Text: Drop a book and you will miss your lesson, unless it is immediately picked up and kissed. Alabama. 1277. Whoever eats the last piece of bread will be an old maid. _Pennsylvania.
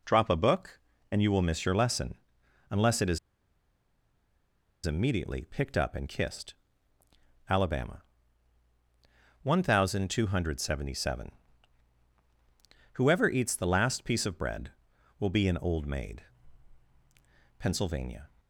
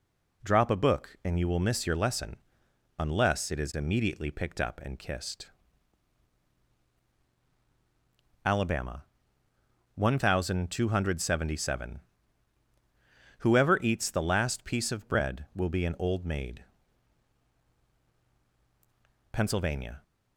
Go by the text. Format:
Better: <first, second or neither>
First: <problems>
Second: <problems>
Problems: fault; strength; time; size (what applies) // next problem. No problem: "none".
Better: second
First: pauses between "is" and "immediately"; strong; at 3.1 s; 1.6 s long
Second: none